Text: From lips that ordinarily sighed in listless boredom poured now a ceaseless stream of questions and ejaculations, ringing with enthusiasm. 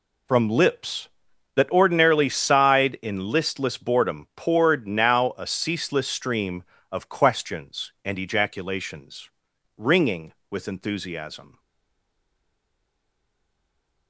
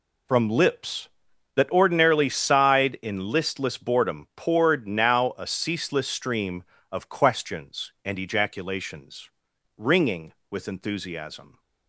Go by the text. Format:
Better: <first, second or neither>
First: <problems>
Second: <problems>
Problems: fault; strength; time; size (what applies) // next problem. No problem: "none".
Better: second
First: stays silent after the last word; strong; from 11.5 s on; 2.5 s long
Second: none